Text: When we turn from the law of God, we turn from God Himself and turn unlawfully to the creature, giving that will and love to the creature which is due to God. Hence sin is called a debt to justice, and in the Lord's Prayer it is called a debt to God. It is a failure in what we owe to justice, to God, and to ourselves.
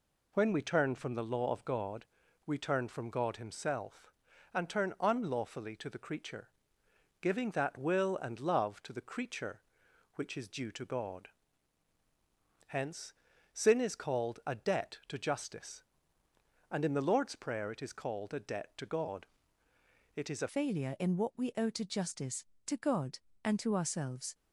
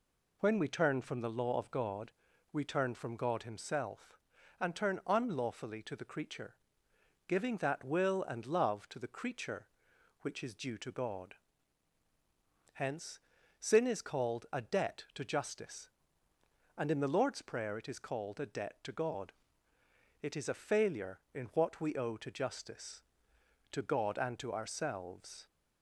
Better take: second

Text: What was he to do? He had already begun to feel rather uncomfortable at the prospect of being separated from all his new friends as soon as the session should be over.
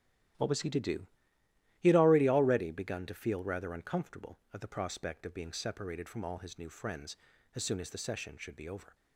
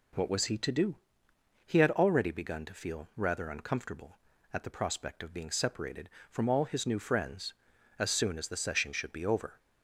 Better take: second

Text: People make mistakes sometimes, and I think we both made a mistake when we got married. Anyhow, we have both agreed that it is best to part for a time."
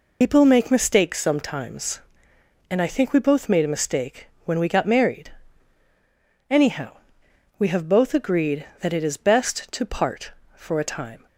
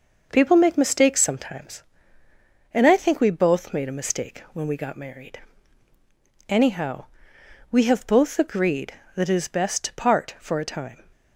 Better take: second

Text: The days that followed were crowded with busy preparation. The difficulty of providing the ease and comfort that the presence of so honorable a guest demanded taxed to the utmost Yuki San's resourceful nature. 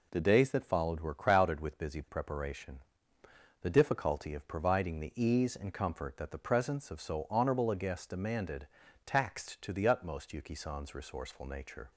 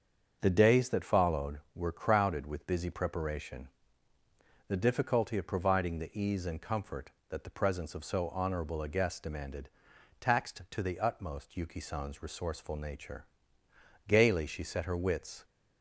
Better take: first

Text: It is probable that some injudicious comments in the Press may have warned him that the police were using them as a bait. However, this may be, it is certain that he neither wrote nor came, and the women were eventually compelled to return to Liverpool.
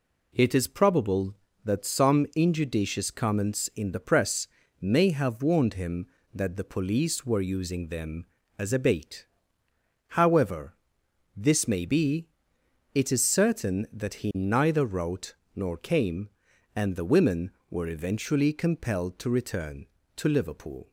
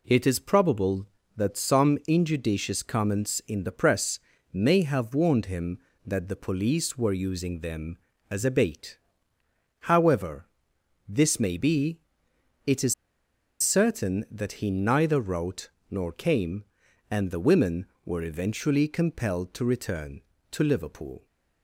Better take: first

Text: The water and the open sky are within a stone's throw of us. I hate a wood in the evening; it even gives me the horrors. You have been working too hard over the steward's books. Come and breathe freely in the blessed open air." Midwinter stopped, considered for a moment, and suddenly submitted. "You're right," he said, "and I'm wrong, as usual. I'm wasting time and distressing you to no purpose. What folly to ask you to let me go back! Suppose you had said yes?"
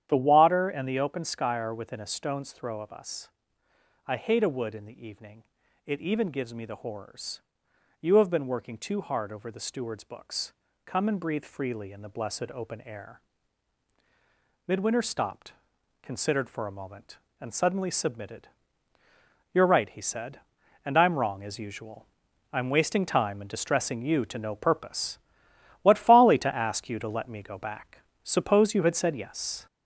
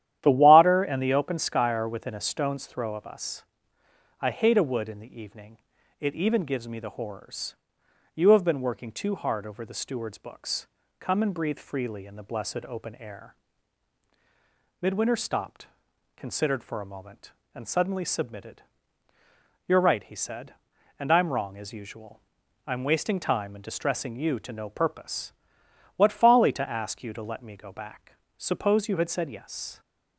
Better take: second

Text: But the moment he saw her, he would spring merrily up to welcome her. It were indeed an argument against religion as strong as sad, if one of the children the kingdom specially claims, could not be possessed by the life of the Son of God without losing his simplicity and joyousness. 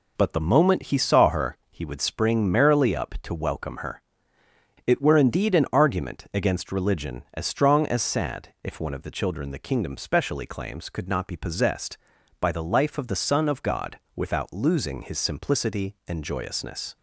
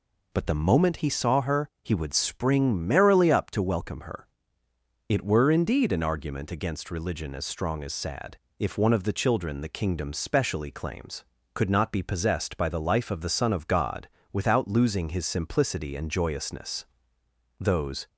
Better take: first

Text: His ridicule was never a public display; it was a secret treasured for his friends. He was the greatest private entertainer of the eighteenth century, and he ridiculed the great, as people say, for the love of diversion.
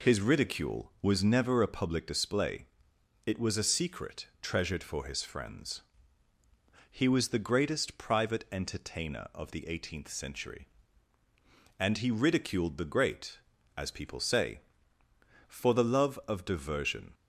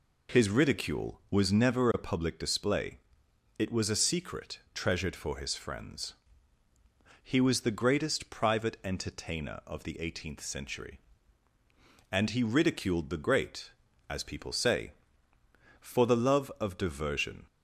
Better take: neither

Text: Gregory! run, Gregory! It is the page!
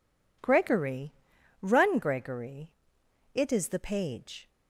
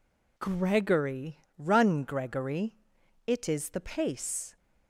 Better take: first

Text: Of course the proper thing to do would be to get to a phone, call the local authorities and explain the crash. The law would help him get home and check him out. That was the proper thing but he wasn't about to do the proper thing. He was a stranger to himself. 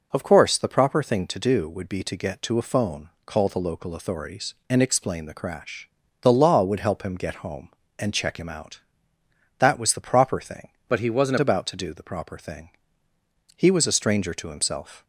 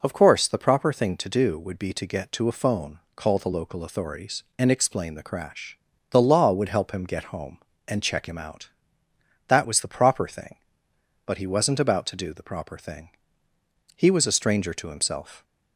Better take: second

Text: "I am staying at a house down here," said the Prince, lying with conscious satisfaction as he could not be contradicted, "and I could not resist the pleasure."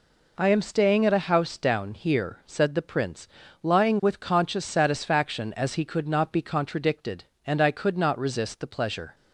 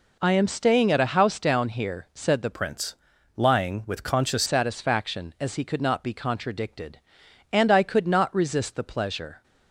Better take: first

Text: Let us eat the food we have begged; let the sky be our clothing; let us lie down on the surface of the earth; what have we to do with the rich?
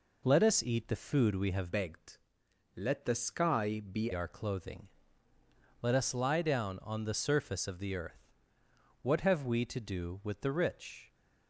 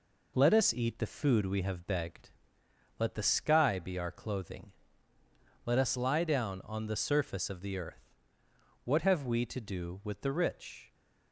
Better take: second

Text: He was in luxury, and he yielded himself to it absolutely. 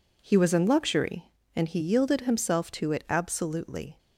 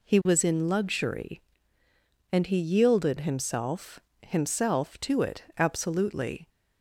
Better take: first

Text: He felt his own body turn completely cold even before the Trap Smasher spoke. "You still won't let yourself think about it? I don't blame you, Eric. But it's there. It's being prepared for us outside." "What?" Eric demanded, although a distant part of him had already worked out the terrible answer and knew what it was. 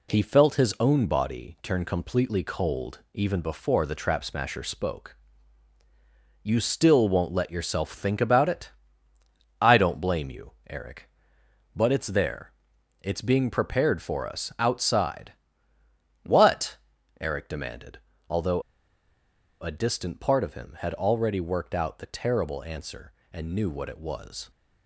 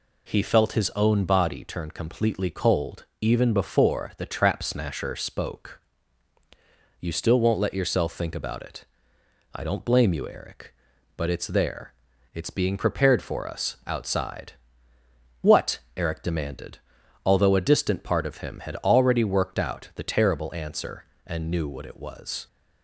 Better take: second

